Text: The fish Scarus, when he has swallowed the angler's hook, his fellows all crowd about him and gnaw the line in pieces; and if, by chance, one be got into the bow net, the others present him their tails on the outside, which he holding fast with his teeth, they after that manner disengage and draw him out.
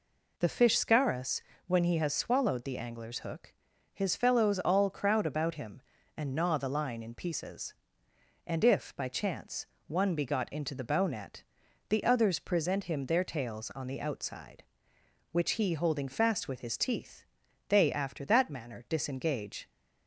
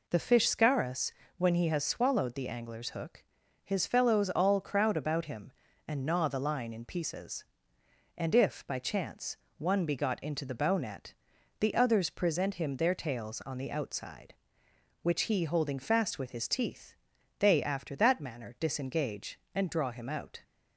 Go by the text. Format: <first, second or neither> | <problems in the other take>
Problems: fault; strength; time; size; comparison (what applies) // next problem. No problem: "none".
second | stops before "and draw him out"; at 19.7 s